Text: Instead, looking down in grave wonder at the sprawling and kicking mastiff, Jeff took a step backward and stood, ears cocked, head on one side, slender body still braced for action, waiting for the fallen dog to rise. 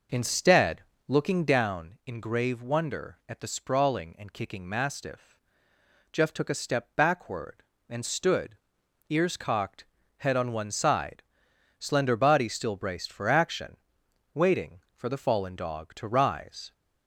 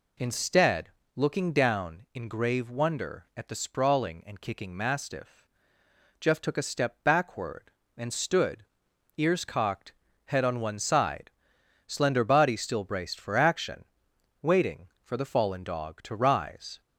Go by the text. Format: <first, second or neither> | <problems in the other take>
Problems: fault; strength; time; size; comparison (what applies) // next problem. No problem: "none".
second | starts louder than the rest; noticeable; until 1.5 s; 5.5 dB